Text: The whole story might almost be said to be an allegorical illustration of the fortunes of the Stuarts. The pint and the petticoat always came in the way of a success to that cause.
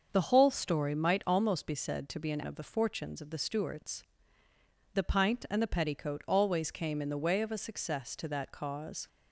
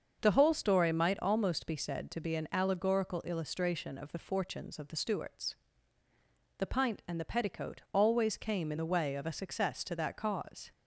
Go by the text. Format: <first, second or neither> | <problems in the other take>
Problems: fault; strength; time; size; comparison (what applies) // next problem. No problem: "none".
second | starts louder than the rest; until 1.1 s; 6.5 dB; also in the second // skips "allegorical illustration"; at 2.4 s